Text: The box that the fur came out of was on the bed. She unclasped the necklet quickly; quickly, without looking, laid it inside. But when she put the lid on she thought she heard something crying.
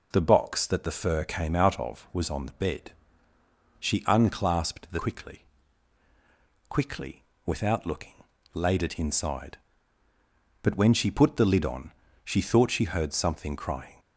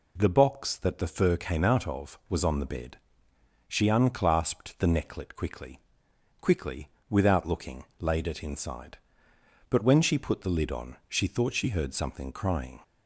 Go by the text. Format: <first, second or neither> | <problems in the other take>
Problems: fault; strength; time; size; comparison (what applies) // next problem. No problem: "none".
second | skips "necklet"; at 4.9 s // pauses between "on" and "she"; slight; at 11.9 s; 0.34 s long